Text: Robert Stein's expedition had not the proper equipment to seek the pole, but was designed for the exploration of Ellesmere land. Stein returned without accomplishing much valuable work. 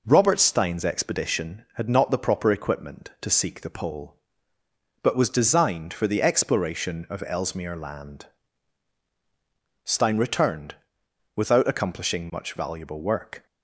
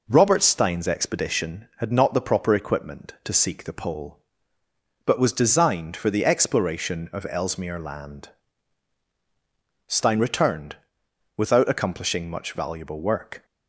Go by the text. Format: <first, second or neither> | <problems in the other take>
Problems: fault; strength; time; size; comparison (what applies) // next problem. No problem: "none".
neither | pauses between "returned" and "without"; noticeable; the same in both